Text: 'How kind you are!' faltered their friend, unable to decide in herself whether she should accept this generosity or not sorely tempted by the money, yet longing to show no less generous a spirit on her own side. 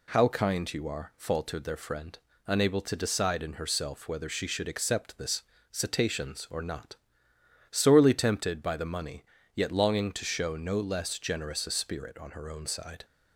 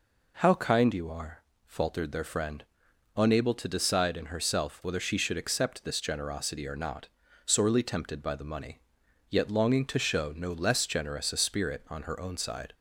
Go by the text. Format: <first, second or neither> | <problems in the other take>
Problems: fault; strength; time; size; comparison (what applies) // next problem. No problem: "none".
second | says "cetaceans" for "generosity"; at 5.7 s // pauses between "not" and "sorely"; noticeable; at 6.9 s; 0.74 s long; also in the second